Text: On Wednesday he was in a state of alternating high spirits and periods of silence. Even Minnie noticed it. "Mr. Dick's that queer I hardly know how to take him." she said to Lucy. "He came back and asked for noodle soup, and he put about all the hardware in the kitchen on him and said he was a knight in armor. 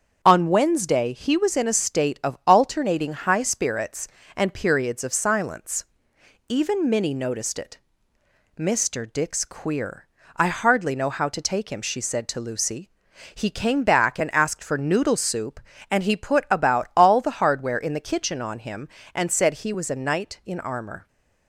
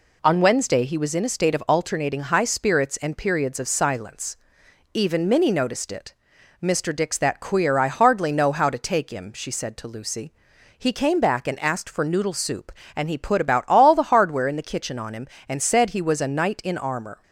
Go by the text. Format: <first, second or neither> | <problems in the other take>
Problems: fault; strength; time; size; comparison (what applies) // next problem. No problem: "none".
second | starts louder than the rest; strong; until 1.2 s; 7.5 dB // skips "that"; at 9.4 s // pauses between "queer" and "I"; slight; at 10.0 s; 0.30 s long